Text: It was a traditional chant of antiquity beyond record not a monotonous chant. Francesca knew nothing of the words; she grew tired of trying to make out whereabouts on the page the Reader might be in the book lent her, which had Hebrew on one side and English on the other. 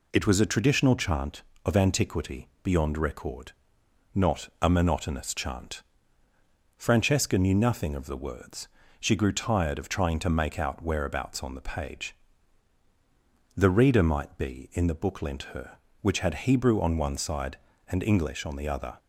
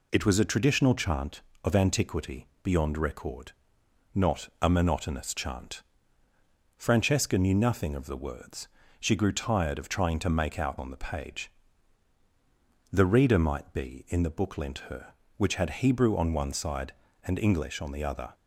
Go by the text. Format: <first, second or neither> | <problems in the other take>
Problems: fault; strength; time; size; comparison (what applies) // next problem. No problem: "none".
first | pauses between "antiquity" and "beyond"; slight; at 2.4 s; 0.16 s long // pauses between "record" and "not"; noticeable; at 3.5 s; 0.60 s long; noticeable in the first // skips "whereabouts"; at 10.7 s // pauses between "page" and "the"; strong; at 11.5 s; 1.4 s long; strong in the first